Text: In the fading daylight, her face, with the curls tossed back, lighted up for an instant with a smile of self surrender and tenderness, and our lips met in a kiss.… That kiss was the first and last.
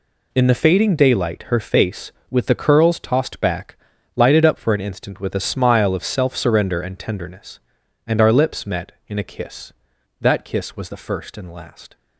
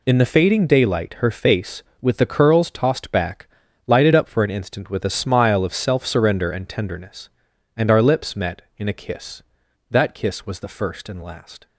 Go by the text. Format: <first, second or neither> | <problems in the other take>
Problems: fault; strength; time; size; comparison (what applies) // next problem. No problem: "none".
neither | none